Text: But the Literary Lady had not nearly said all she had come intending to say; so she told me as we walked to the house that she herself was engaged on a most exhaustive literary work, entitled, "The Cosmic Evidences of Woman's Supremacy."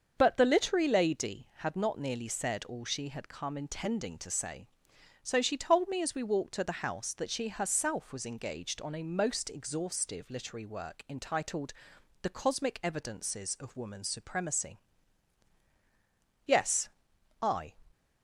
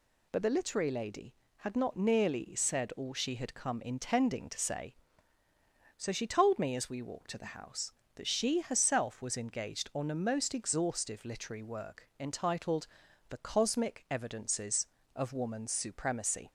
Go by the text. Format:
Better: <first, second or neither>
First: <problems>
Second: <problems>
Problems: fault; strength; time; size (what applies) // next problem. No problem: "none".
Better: second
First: starts louder than the rest; until 1.1 s; 6.5 dB // goes on to say "Yes I"; noticeable; from 16.4 s on; 1.2 s long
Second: none